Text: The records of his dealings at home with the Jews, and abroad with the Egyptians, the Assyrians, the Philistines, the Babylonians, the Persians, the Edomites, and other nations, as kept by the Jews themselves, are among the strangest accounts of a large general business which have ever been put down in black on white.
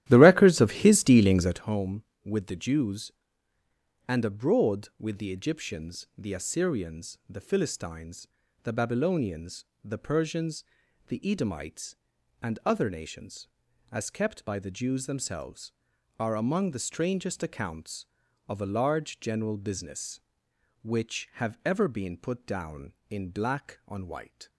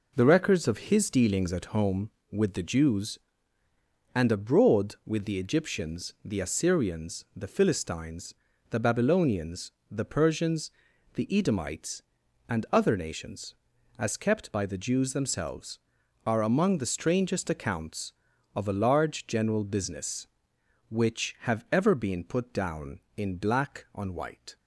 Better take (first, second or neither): second